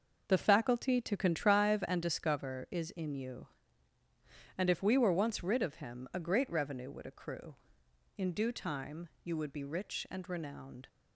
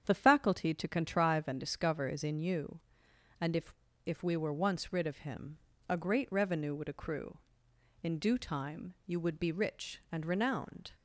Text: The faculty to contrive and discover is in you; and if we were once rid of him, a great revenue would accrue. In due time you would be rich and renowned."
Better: first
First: none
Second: starts louder than the rest; strong; until 1.0 s; 8.5 dB // says "if" twice; at 4.0 s

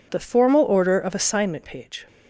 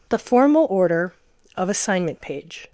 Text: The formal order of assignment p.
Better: neither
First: none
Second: none

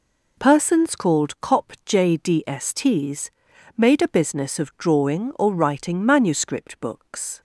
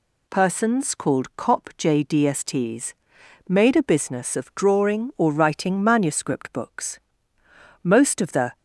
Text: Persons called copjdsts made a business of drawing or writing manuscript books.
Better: first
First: pauses between "copjdsts" and "made"; noticeable; at 3.3 s; 0.46 s long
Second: pauses between "copjdsts" and "made"; noticeable; at 2.9 s; 0.54 s long // goes on to say "Most of the"; noticeable; from 7.8 s on; 0.76 s long

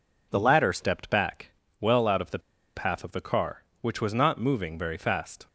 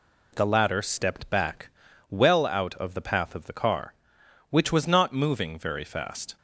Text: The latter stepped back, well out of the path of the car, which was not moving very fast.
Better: second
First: pauses between "the" and "path"; at 2.3 s; 0.36 s long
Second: none

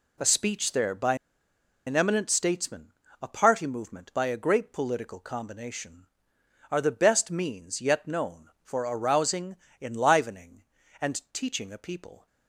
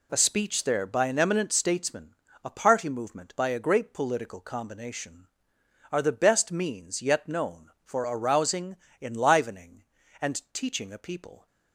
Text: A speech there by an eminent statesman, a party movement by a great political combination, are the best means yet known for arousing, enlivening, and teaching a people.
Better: second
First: pauses between "by" and "an"; noticeable; at 1.1 s; 0.71 s long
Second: none

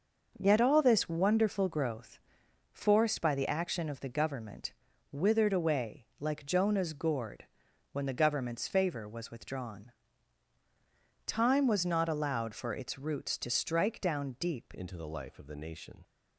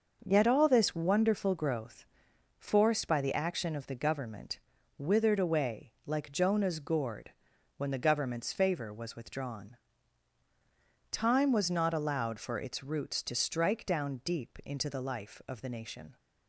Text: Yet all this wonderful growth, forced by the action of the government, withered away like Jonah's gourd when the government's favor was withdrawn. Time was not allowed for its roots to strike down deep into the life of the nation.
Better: second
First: starts louder than the rest; noticeable; until 1.3 s; 6 dB // pauses between "gourd" and "when"; noticeable; at 7.4 s; 0.48 s long // changes voice at "into"; from 14.7 s on; 1.3 s long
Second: starts louder than the rest; noticeable; until 1.2 s; 6 dB // pauses between "gourd" and "when"; noticeable; at 7.3 s; 0.46 s long

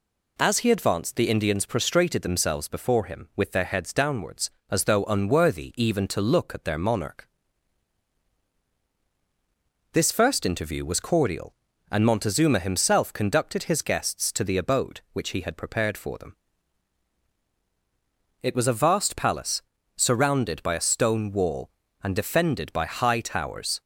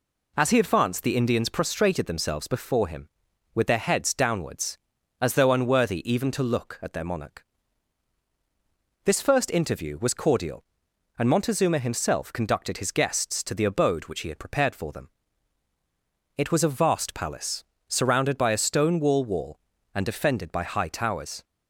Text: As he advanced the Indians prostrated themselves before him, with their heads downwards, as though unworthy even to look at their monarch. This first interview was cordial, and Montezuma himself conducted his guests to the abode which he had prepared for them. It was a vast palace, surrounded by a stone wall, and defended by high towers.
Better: first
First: none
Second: says "wall" twice; at 19.2 s

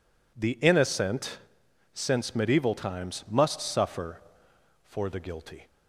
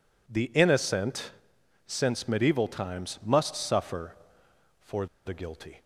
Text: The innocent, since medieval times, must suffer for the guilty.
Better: first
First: none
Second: pauses between "for" and "the"; slight; at 5.0 s; 0.19 s long

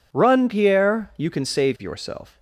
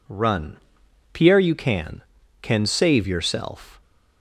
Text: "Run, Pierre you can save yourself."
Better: first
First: none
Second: says "can" twice; at 2.4 s

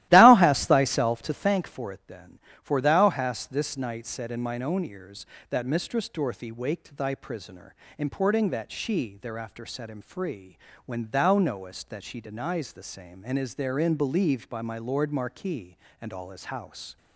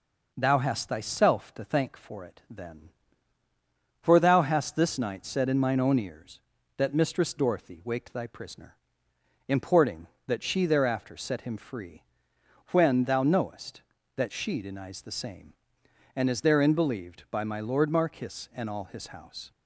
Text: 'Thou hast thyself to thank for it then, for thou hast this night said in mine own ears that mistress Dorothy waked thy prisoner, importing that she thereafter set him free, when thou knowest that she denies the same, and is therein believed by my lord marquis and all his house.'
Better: second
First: starts louder than the rest; strong; until 1.6 s; 15.5 dB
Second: none

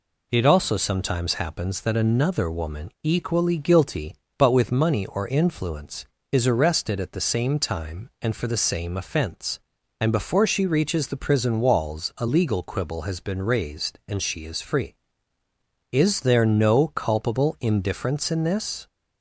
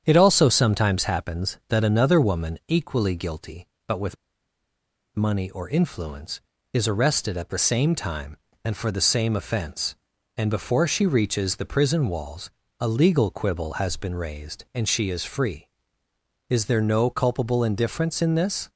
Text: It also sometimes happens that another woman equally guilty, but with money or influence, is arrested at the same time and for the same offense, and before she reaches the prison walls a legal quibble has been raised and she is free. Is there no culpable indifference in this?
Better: first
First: none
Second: starts louder than the rest; strong; until 1.0 s; 8.5 dB // pauses between "with" and "money"; at 4.1 s; 1.0 s long // pauses between "walls" and "a"; slight; at 12.5 s; 0.28 s long

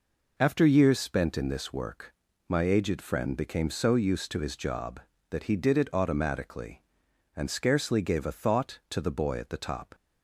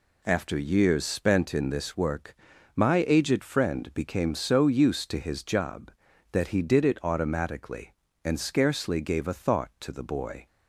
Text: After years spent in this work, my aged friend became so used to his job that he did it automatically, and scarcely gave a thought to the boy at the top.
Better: first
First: none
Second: stops before "at the top"; at 10.4 s

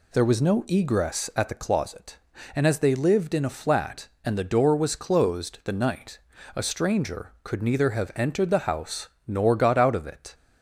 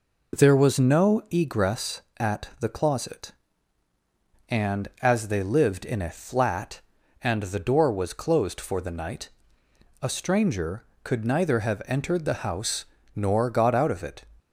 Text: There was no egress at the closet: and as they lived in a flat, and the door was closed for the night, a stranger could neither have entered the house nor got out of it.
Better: second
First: skips "for"; at 5.6 s // pauses between "house" and "nor"; slight; at 9.0 s; 0.20 s long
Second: pauses between "house" and "nor"; slight; at 12.8 s; 0.30 s long

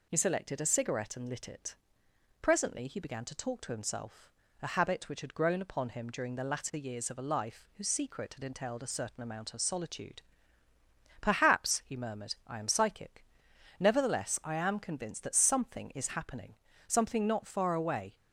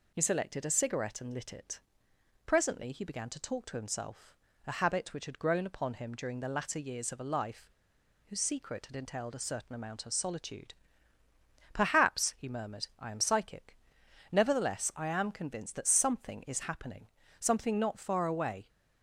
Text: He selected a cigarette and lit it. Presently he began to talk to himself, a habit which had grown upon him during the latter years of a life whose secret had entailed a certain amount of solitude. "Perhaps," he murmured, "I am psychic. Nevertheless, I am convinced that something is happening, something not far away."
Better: first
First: none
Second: pauses between "life" and "whose"; noticeable; at 7.7 s; 0.56 s long

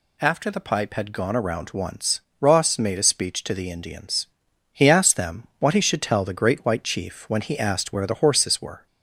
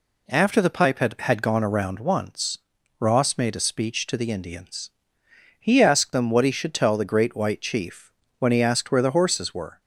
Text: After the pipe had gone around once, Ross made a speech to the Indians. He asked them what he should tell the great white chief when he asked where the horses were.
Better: first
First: none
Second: says "had" twice; at 1.1 s // pauses between "chief" and "when"; slight; at 8.1 s; 0.28 s long

